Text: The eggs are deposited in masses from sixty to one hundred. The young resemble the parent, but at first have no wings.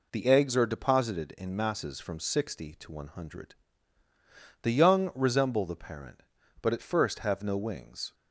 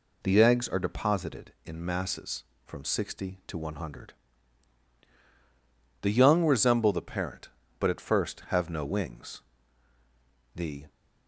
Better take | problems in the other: first | goes on to say "The"; slight; from 10.5 s on; 0.30 s long

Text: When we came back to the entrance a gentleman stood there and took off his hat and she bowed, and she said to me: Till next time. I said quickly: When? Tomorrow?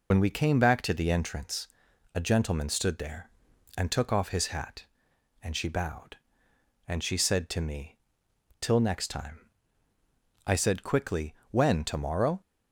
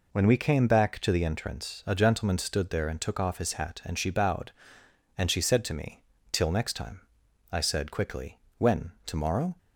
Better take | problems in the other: second | loses the start of "When"; at 0.1 s; 60 ms // pauses between "entrance" and "a"; noticeable; at 1.6 s; 0.48 s long

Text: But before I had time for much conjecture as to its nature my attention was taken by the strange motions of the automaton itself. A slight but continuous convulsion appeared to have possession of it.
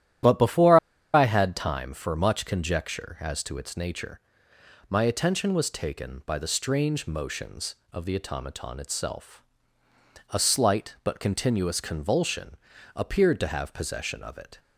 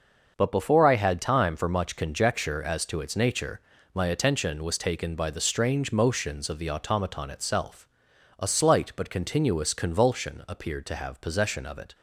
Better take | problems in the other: second | starts louder than the rest; strong; until 1.5 s; 11.5 dB; noticeable in the second // pauses between "before" and "I"; slight; at 0.7 s; 0.35 s long // pauses between "nature" and "my"; noticeable; at 4.1 s; 0.70 s long; slight in the second // pauses between "convulsion" and "appeared"; slight; at 12.5 s; 0.36 s long

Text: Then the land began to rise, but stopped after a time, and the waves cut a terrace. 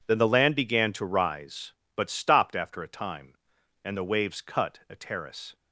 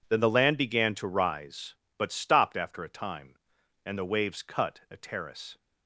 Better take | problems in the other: neither | none

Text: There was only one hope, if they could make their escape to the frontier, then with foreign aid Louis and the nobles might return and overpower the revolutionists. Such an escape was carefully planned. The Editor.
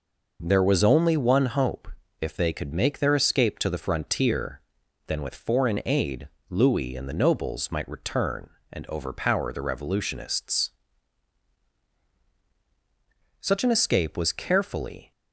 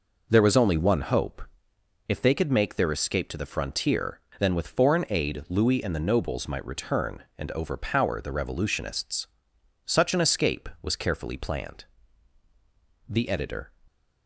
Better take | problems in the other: second | pauses between "aid" and "Louis"; slight; at 6.2 s; 0.20 s long // stops before "planned The Editor"; at 15.1 s

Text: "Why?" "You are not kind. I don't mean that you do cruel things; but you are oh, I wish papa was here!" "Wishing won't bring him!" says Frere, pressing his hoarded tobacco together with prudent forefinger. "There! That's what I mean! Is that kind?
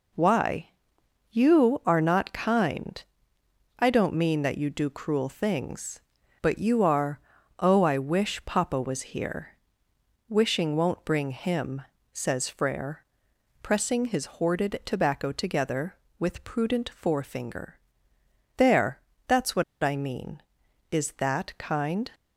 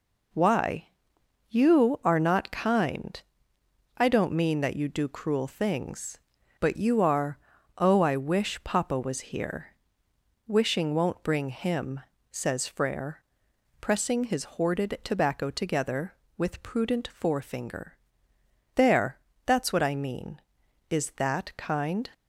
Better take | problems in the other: second | pauses between "are" and "oh"; at 7.1 s; 0.40 s long; also in the second // pauses between "what" and "I"; slight; at 19.6 s; 0.18 s long

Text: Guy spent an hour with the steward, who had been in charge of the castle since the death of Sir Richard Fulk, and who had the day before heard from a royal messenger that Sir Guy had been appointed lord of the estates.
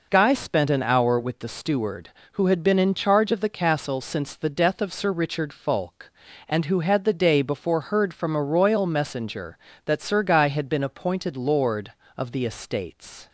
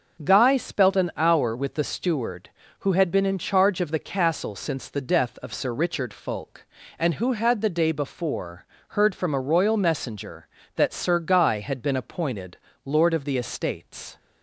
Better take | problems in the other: first | starts louder than the rest; until 1.2 s; 6.5 dB // says "spelt" for "spent"; at 0.5 s // pauses between "before" and "heard"; slight; at 8.6 s; 0.24 s long // pauses between "appointed" and "lord"; slight; at 12.5 s; 0.26 s long

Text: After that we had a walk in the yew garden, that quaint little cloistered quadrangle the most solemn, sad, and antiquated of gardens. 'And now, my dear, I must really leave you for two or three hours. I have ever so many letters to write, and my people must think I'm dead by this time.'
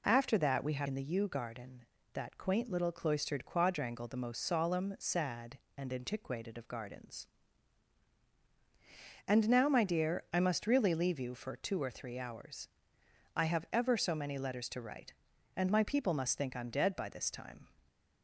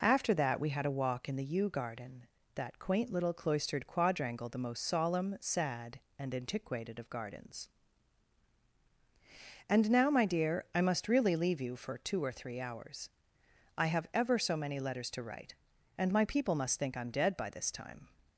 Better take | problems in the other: second | skips "a walk"; at 0.8 s

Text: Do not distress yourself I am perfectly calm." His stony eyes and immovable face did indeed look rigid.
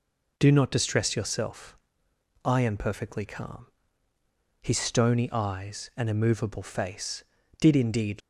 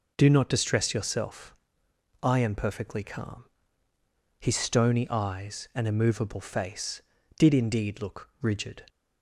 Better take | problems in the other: second | pauses between "yourself" and "I"; noticeable; at 1.7 s; 0.66 s long; noticeable in the second // stops before "look rigid"; at 8.2 s

